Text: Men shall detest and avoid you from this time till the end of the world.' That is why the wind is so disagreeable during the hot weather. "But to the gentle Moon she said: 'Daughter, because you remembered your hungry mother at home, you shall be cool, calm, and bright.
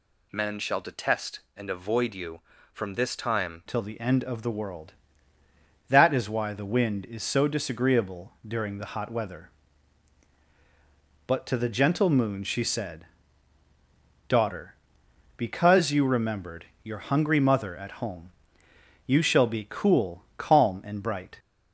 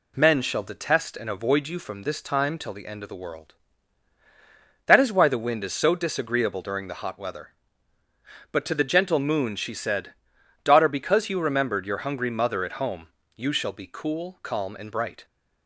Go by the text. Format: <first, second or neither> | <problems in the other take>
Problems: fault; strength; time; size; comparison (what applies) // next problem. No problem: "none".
second | changes voice at "till"; from 3.6 s on; 17.7 s long // pauses between "disagreeable" and "during"; slight; at 8.3 s; 0.16 s long // pauses between "remembered" and "your"; slight; at 16.6 s; 0.18 s long